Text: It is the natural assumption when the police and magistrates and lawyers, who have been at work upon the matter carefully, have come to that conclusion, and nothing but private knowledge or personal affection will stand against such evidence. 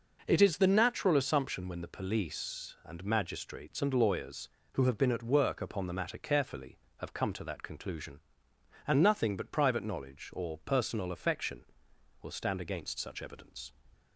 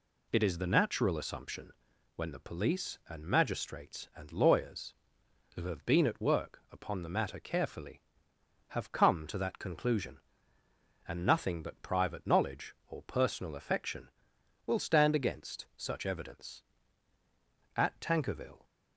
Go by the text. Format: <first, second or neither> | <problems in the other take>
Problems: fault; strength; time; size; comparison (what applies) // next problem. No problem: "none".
first | pauses between "assumption" and "when"; at 1.7 s; 0.44 s long // goes on to say "At Tankerville"; noticeable; from 17.7 s on; 0.90 s long